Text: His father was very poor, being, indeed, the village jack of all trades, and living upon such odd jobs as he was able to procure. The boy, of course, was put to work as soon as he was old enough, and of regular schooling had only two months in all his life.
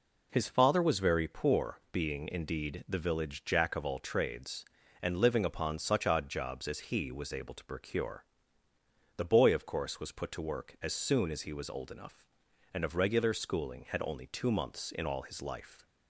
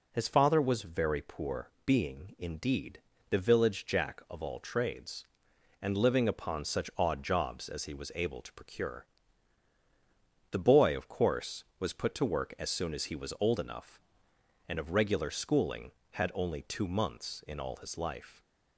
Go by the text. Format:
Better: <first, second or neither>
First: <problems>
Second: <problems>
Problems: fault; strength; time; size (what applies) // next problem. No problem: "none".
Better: neither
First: none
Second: none